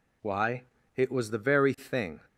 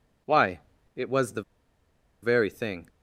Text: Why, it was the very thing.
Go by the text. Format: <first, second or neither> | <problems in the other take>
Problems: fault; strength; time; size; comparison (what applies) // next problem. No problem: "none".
first | pauses between "the" and "very"; noticeable; at 1.4 s; 0.80 s long